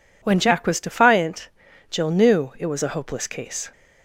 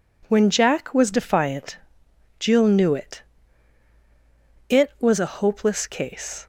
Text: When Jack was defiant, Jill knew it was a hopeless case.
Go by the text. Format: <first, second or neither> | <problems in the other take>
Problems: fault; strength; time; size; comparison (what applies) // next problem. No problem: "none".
first | says "it" twice; at 4.6 s